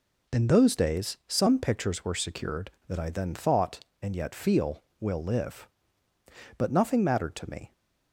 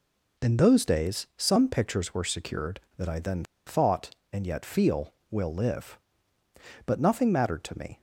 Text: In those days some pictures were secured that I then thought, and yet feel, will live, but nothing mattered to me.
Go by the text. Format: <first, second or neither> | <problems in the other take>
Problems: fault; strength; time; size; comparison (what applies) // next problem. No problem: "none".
first | pauses between "then" and "thought"; slight; at 3.4 s; 0.23 s long